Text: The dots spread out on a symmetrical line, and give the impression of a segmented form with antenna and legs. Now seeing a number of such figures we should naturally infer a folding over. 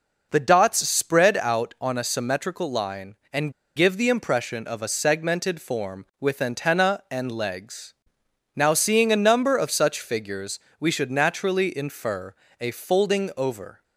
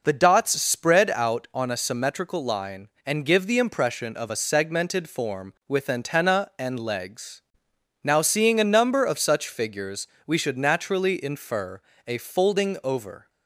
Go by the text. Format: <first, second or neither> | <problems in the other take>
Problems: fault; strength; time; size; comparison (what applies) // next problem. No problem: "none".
second | pauses between "and" and "give"; slight; at 3.5 s; 0.25 s long // pauses between "figures" and "we"; slight; at 10.5 s; 0.20 s long; slight in the second // pauses between "infer" and "a"; slight; at 12.3 s; 0.26 s long; slight in the second